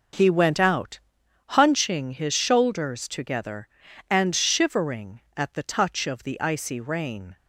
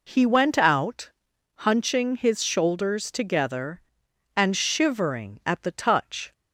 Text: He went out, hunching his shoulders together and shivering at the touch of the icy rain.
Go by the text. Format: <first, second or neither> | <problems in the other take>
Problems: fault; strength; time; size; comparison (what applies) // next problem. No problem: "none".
first | stops before "of the icy rain"; at 6.3 s